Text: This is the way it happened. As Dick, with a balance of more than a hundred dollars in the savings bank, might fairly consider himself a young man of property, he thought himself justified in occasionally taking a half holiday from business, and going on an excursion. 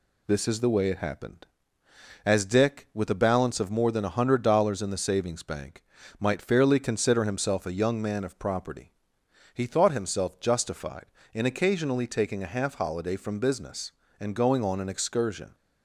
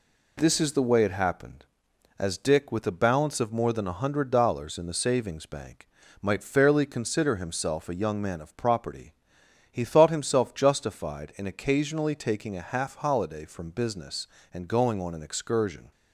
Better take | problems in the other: neither | none

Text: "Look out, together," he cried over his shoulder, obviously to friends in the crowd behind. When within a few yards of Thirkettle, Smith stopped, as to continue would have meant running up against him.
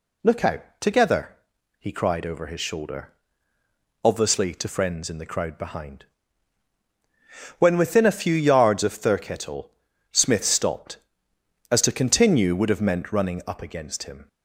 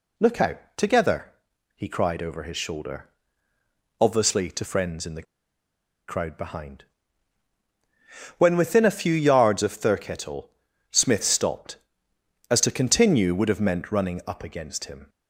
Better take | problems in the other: first | pauses between "the" and "crowd"; noticeable; at 5.2 s; 0.85 s long

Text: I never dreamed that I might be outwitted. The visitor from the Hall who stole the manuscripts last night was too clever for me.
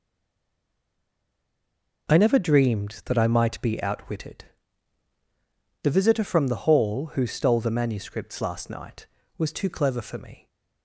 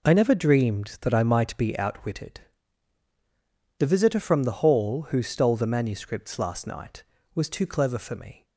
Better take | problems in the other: second | stays silent before the first word; noticeable; until 2.0 s; 2.0 s long

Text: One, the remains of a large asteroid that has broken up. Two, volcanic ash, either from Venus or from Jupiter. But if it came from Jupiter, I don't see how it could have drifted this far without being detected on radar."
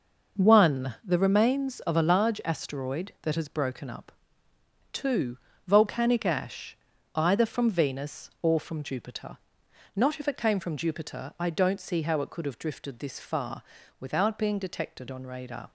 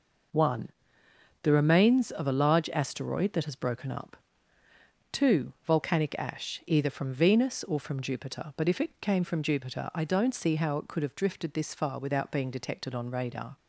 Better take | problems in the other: second | says "Not" for "But"; at 9.9 s // pauses between "far" and "without"; slight; at 13.6 s; 0.36 s long

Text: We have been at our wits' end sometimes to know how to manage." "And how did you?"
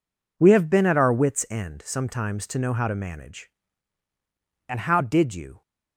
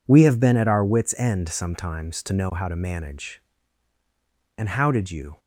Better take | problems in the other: neither | none

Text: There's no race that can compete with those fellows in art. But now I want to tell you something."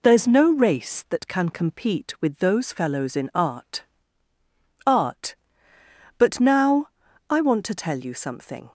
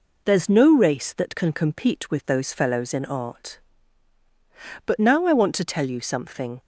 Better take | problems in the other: second | says "art" twice; at 4.8 s // pauses between "now" and "I"; at 6.8 s; 0.42 s long

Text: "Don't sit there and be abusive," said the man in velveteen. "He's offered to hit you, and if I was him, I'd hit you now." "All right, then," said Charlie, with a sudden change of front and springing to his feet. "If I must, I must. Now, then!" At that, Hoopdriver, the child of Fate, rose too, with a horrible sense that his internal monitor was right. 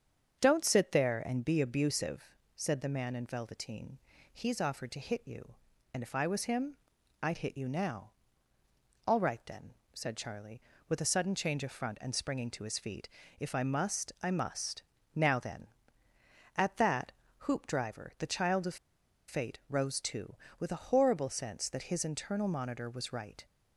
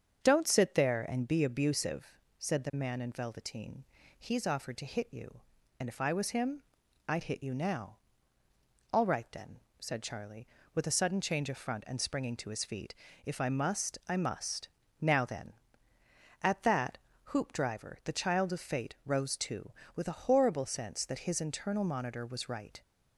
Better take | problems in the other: second | starts louder than the rest; strong; until 1.4 s; 7 dB; strong in the second // pauses between "of" and "Fate"; noticeable; at 18.7 s; 0.52 s long

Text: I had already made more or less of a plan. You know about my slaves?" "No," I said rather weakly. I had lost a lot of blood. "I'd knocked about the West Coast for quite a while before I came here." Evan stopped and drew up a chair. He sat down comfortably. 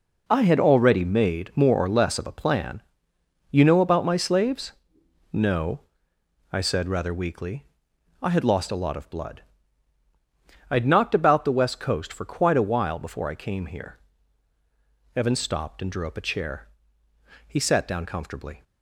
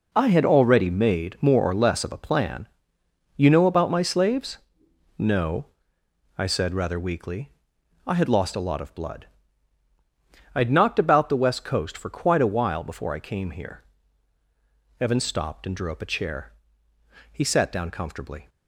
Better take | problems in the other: neither | none

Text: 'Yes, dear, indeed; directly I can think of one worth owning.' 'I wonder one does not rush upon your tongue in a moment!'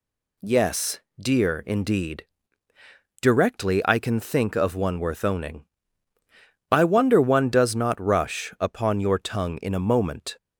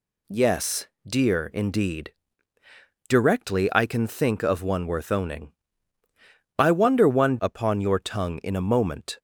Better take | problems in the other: first | skips "does not rush"; at 7.3 s

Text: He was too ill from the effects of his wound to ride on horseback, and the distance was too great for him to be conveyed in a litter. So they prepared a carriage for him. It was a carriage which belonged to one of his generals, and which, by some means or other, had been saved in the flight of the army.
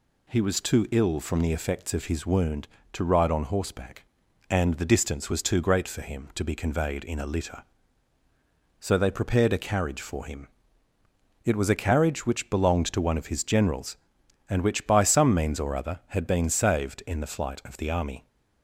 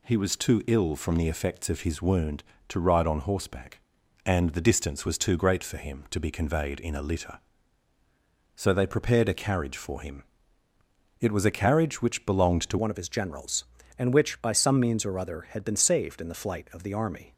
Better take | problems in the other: first | changes voice at "one"; from 12.7 s on; 4.6 s long

